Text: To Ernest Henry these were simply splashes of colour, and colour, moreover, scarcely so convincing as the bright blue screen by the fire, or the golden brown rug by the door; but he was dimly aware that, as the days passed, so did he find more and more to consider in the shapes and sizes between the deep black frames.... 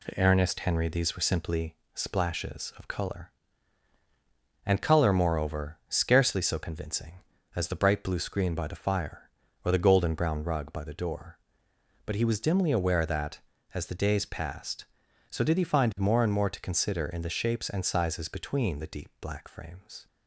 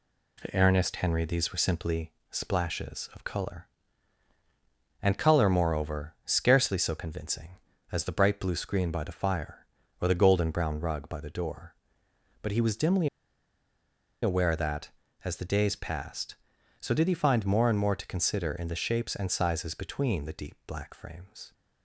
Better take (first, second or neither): first